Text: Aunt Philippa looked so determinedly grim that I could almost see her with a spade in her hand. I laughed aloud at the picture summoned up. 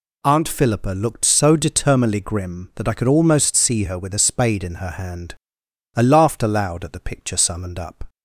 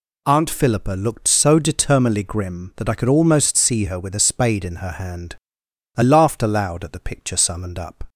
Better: neither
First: none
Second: none

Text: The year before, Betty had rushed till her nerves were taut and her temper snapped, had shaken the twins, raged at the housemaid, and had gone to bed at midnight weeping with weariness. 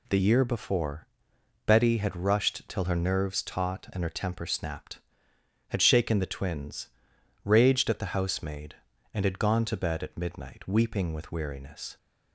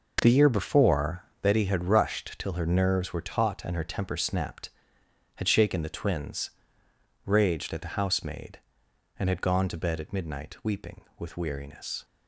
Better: second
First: skips "were"; at 3.4 s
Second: none

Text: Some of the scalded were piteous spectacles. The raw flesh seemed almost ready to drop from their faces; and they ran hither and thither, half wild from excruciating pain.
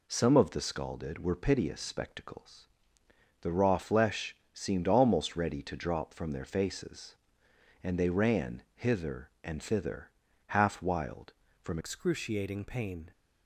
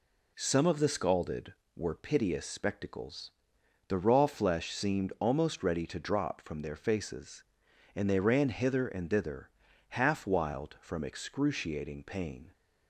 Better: second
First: pauses between "flesh" and "seemed"; slight; at 4.3 s; 0.16 s long // changes voice at "excruciating"; from 11.7 s on; 1.4 s long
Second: none

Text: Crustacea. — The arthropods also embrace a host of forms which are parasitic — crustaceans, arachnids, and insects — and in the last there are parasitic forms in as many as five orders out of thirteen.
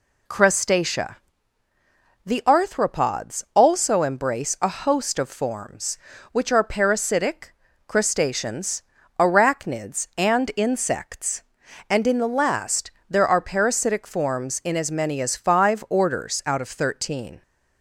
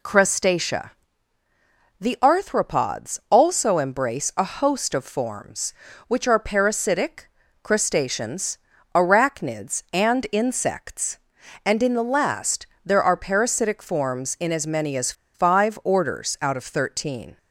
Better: first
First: pauses between "last" and "there"; slight; at 12.9 s; 0.18 s long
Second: pauses between "last" and "there"; slight; at 12.6 s; 0.18 s long // pauses between "as" and "five"; slight; at 15.1 s; 0.22 s long

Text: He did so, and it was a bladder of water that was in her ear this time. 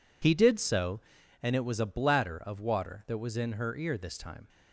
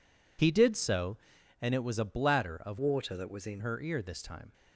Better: first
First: none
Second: changes voice from "water" to "in"; from 2.7 to 3.6 s; 0.9 s long

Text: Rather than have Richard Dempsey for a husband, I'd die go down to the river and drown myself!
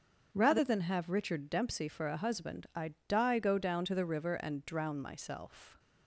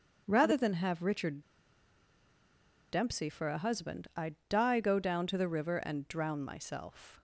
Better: first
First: starts louder than the rest; until 1.3 s; 7 dB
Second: starts louder than the rest; until 1.2 s; 7 dB // pauses between "Richard" and "Dempsey"; strong; at 1.4 s; 1.4 s long

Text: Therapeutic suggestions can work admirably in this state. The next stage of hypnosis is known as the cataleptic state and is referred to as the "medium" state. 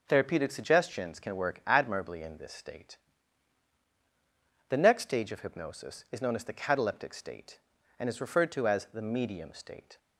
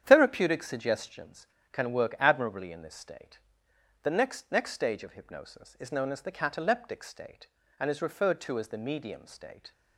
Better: first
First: none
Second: starts louder than the rest; strong; until 1.0 s; 9 dB // says "next" twice; at 4.5 s

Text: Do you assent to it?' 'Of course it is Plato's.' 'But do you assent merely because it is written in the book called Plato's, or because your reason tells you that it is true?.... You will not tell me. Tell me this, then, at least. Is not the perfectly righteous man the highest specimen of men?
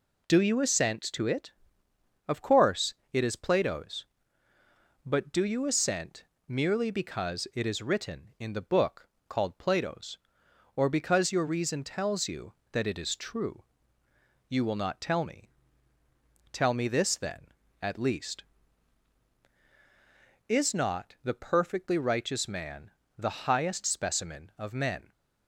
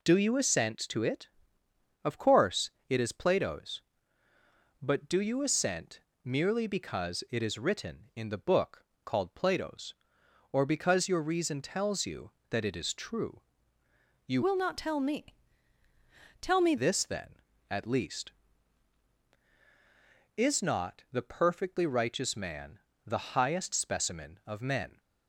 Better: first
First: pauses between "course" and "it"; slight; at 2.9 s; 0.18 s long // pauses between "assent" and "merely"; slight; at 6.2 s; 0.24 s long // pauses between "book" and "called"; slight; at 9.0 s; 0.18 s long // pauses between "man" and "the"; slight; at 22.9 s; 0.26 s long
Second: pauses between "course" and "it"; slight; at 2.7 s; 0.18 s long // pauses between "assent" and "merely"; slight; at 6.0 s; 0.24 s long // pauses between "book" and "called"; slight; at 8.8 s; 0.18 s long // changes voice from "will" to "me"; from 14.4 to 16.7 s; 2.3 s long // pauses between "man" and "the"; slight; at 22.7 s; 0.26 s long

